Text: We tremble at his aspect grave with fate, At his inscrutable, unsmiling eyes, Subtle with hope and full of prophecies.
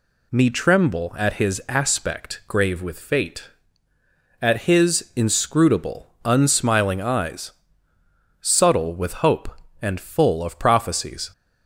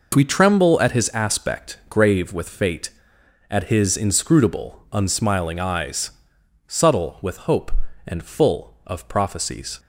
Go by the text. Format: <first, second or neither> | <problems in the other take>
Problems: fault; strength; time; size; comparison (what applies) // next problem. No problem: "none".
second | says "Me" for "We"; at 0.3 s